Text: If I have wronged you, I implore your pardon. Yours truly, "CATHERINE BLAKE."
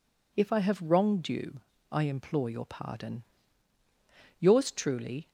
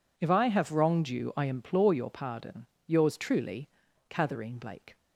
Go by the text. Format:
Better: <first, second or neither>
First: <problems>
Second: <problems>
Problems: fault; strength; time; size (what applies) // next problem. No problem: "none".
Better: second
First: stops before "CATHERINE BLAKE"; at 5.2 s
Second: none